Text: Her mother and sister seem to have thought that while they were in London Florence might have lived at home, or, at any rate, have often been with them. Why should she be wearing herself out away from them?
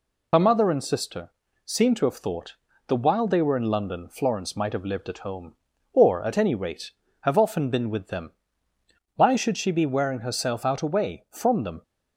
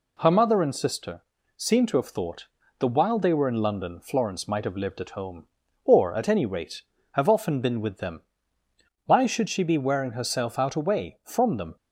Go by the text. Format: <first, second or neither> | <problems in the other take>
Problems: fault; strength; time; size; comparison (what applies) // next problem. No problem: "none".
second | loses the start of "Her"; at 0.3 s; 60 ms // pauses between "sister" and "seem"; slight; at 1.3 s; 0.34 s long; slight in the second